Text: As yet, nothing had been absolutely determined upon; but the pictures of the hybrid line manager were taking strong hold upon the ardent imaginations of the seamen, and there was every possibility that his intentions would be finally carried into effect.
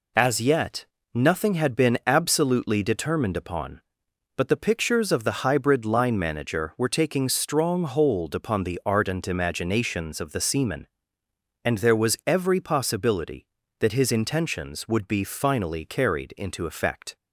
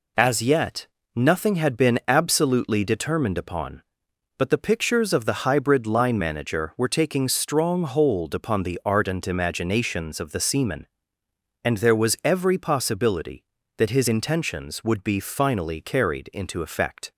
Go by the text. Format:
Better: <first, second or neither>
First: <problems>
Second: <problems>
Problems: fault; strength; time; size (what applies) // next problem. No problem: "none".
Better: neither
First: none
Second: none